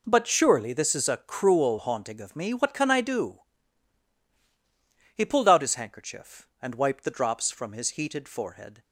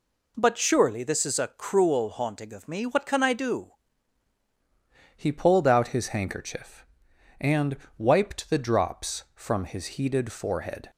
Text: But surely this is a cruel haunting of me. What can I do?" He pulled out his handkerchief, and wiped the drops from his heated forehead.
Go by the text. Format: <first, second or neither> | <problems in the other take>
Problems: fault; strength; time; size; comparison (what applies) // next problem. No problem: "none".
first | changes voice at "He"; from 5.1 s on; 5.7 s long // pauses between "and" and "wiped"; slight; at 7.7 s; 0.20 s long